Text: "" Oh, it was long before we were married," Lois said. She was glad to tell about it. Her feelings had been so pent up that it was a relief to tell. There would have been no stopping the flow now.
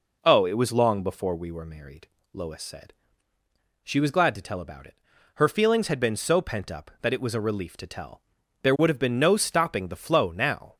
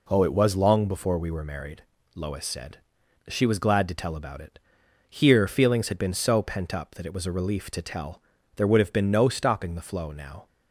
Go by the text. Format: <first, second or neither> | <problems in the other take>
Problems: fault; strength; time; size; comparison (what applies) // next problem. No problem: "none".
first | says "Here" for "Her"; at 5.0 s